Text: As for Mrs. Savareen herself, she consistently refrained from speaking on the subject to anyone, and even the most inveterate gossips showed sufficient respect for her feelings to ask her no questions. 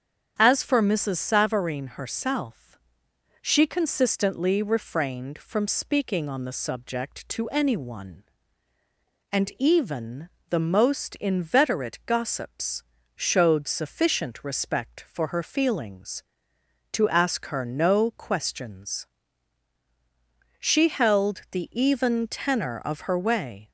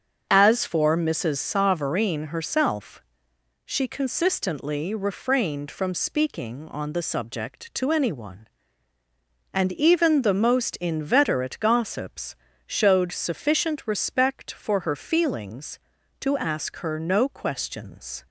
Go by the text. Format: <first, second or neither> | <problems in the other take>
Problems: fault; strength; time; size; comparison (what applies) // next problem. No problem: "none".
second | starts louder than the rest; strong; until 1.3 s; 8 dB; also in the second // pauses between "even" and "the"; slight; at 10.2 s; 0.22 s long // pauses between "gossips" and "showed"; slight; at 12.8 s; 0.32 s long; slight in the second // goes on to say "She held the even tenor of her way"; strong; from 20.6 s on; 3.1 s long